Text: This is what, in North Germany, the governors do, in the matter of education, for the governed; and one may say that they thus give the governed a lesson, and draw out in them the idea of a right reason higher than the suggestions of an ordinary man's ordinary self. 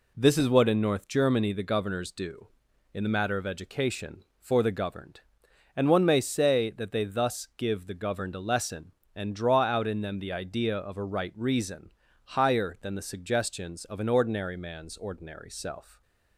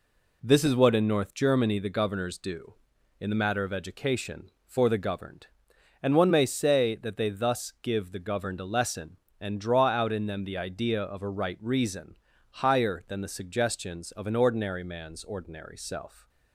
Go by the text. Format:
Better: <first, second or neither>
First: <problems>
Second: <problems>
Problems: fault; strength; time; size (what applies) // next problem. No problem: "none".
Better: neither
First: pauses between "reason" and "higher"; at 11.9 s; 0.38 s long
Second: pauses between "reason" and "higher"; at 12.1 s; 0.40 s long